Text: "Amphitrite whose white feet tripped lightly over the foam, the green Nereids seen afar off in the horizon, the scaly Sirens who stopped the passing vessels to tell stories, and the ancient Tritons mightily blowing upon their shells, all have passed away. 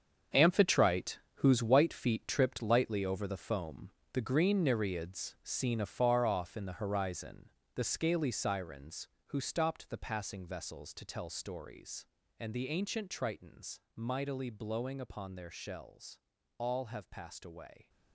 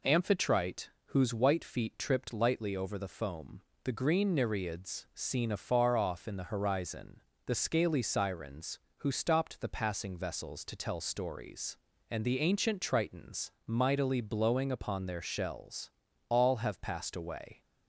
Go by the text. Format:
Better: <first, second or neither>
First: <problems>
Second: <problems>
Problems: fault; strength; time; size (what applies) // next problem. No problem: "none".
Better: second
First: gets quieter; strong; throughout; 11.5 dB // pauses between "Amphitrite" and "whose"; slight; at 1.1 s; 0.20 s long // pauses between "Tritons" and "mightily"; slight; at 13.7 s; 0.16 s long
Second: pauses between "Amphitrite" and "whose"; slight; at 0.8 s; 0.20 s long // pauses between "Tritons" and "mightily"; slight; at 13.4 s; 0.16 s long